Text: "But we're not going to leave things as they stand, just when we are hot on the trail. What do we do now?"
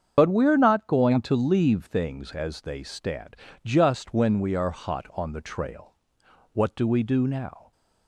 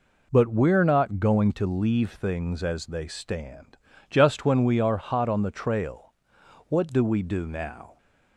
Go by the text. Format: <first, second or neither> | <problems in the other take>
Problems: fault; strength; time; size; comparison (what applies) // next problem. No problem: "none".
second | loses the start of "But"; at 0.1 s; 90 ms // starts louder than the rest; strong; until 1.1 s; 7.5 dB